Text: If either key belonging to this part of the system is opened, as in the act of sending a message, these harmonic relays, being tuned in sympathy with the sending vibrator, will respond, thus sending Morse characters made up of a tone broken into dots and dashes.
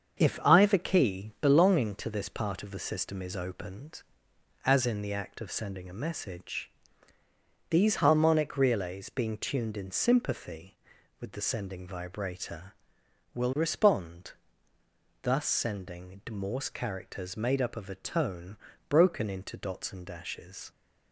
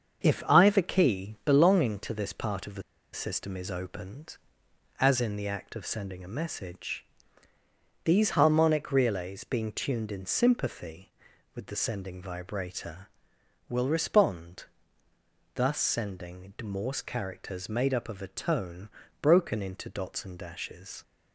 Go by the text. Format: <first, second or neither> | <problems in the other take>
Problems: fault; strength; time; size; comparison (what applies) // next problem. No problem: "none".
first | starts louder than the rest; until 1.2 s; 7 dB; also in the first // pauses between "the" and "system"; slight; at 2.8 s; 0.32 s long // pauses between "tone" and "broken"; slight; at 18.9 s; 0.32 s long; slight in the first